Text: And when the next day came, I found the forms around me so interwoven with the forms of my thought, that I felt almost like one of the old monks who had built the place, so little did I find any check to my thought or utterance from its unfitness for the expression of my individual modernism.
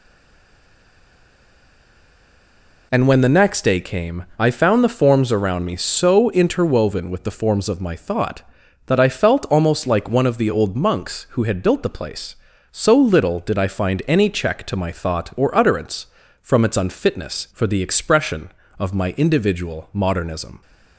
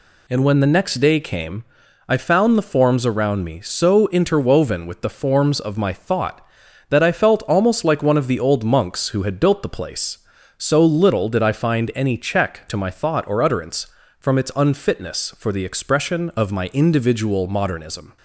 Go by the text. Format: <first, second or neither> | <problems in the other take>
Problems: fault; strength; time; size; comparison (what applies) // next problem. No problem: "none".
second | stays silent before the first word; strong; until 2.9 s; 2.9 s long